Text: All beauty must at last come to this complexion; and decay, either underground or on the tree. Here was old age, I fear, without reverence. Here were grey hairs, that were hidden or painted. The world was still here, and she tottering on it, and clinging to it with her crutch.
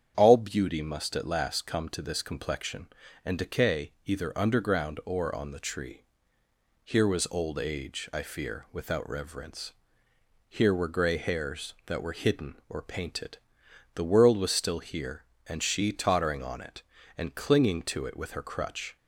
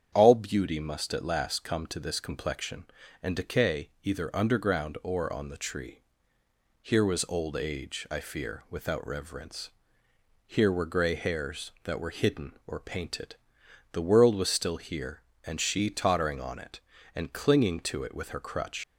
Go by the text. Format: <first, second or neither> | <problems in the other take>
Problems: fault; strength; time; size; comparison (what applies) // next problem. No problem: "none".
first | starts louder than the rest; strong; until 1.1 s; 8 dB; strong in the first // leaves "crutch" unfinished; at 18.8 s; 110 ms